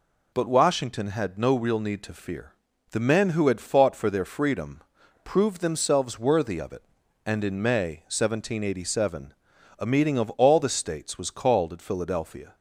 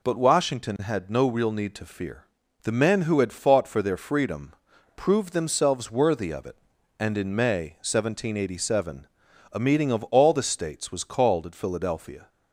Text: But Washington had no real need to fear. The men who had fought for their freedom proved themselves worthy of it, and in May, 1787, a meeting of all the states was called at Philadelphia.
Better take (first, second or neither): neither